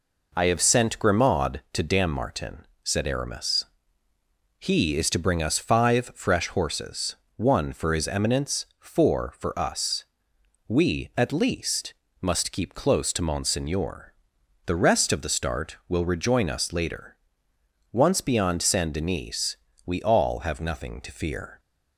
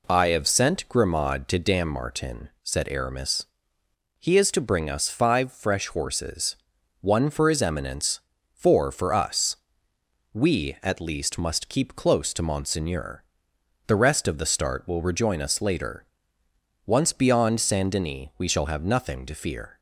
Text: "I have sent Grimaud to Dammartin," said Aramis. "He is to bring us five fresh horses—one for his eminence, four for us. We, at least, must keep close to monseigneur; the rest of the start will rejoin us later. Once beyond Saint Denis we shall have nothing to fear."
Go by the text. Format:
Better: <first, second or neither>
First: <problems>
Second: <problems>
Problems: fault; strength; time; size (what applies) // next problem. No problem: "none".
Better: second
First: pauses between "Denis" and "we"; slight; at 19.5 s; 0.30 s long // says "all" for "shall"; at 20.0 s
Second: none